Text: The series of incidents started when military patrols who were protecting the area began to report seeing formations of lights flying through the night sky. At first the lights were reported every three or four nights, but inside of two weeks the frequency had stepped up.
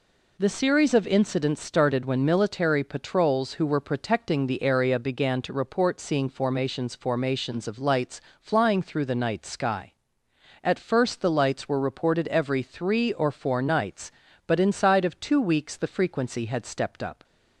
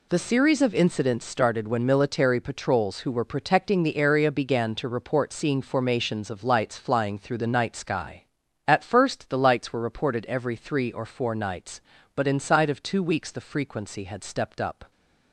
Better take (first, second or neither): second